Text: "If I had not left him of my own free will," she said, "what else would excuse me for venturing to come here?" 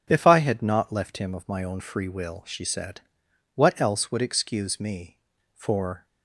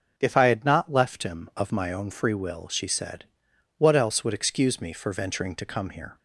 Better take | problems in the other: second | starts louder than the rest; strong; until 1.0 s; 8.5 dB // stops before "venturing to come here"; at 6.0 s

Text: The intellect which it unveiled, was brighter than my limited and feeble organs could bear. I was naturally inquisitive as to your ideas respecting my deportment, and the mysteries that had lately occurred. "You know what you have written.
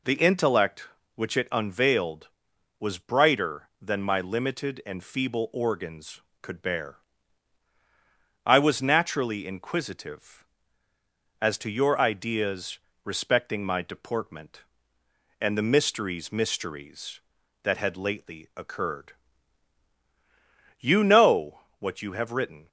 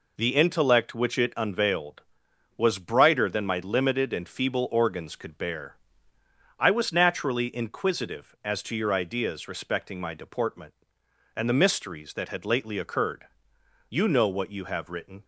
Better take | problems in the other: second | pauses between "ideas" and "respecting"; slight; at 12.7 s; 0.24 s long // says "mysteries" twice; at 16.3 s // pauses between "know" and "what"; slight; at 21.6 s; 0.18 s long

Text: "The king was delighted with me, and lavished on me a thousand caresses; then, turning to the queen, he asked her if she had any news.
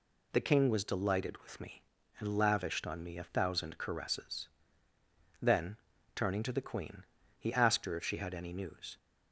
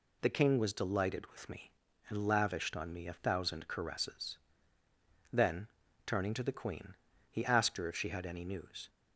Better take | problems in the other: neither | none

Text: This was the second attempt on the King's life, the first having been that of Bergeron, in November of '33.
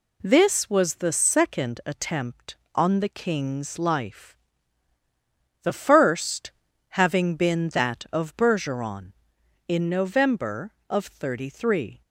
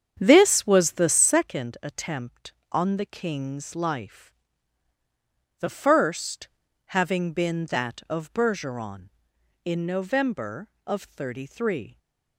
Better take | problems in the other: first | starts louder than the rest; strong; until 1.4 s; 8 dB // pauses between "first" and "having"; at 6.4 s; 0.38 s long; also in the first

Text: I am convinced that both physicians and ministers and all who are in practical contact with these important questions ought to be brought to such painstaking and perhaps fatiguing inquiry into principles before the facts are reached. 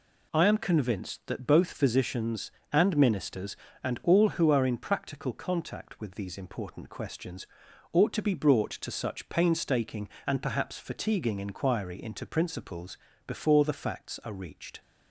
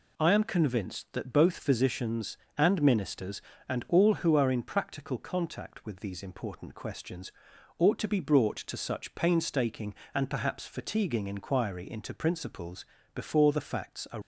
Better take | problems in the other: first | pauses between "questions" and "ought"; noticeable; at 7.3 s; 0.46 s long; also in the first // pauses between "principles" and "before"; slight; at 12.8 s; 0.32 s long; slight in the first // stops before "reached"; at 14.2 s

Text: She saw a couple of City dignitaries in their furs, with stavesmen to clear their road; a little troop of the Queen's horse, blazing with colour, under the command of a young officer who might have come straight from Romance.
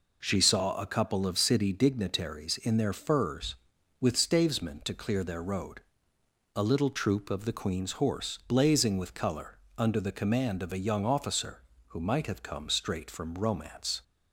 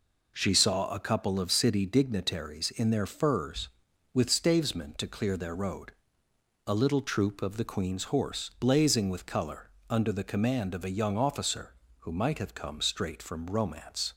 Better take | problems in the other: neither | none

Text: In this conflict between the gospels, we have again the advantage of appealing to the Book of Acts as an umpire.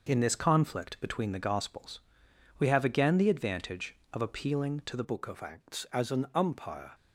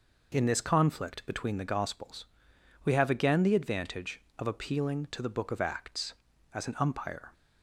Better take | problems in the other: second | changes voice at "Book"; from 5.0 s on; 1.9 s long

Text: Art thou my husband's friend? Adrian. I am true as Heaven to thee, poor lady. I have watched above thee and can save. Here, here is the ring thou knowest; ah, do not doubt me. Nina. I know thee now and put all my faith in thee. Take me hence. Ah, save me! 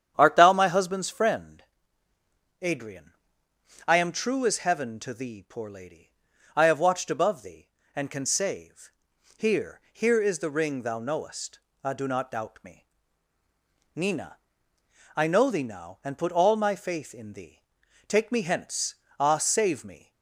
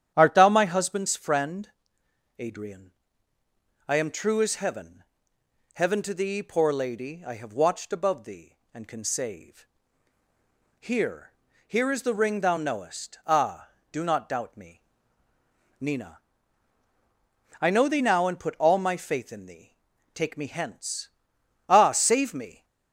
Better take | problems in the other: first | starts louder than the rest; strong; until 1.1 s; 10 dB; strong in the first // says "Heaven" twice; at 5.7 s

